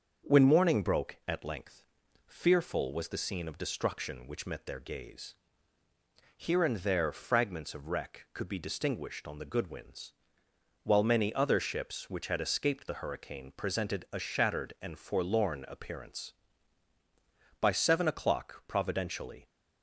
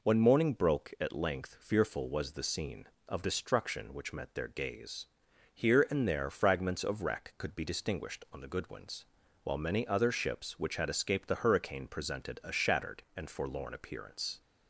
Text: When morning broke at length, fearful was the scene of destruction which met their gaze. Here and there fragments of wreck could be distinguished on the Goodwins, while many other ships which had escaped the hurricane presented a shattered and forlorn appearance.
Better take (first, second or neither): second